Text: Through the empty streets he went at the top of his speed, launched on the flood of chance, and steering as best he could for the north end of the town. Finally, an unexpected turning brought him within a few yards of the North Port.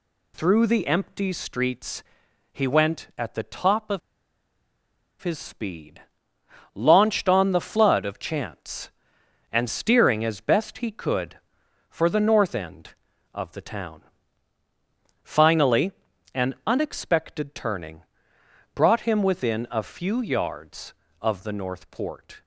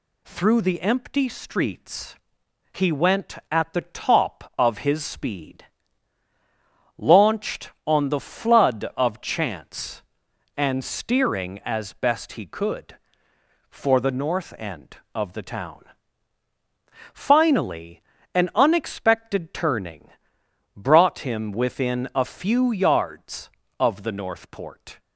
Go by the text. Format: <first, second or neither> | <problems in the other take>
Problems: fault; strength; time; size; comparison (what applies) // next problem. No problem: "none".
second | pauses between "streets" and "he"; noticeable; at 2.0 s; 0.48 s long; noticeable in the second // pauses between "of" and "his"; at 4.0 s; 1.2 s long // pauses between "turning" and "brought"; noticeable; at 18.0 s; 0.72 s long; noticeable in the second